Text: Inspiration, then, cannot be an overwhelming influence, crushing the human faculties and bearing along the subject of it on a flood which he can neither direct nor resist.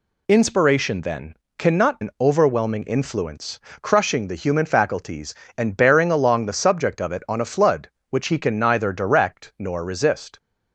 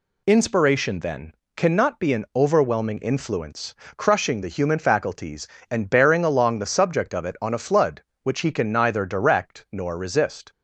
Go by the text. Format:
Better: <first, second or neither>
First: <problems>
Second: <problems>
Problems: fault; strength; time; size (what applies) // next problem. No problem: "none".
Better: second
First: skips "be"; at 2.0 s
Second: none